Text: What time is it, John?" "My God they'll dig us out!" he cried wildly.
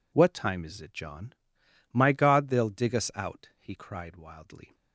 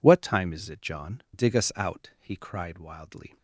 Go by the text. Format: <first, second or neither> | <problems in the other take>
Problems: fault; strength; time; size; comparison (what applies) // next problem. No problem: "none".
first | skips "My God they'll"; at 1.2 s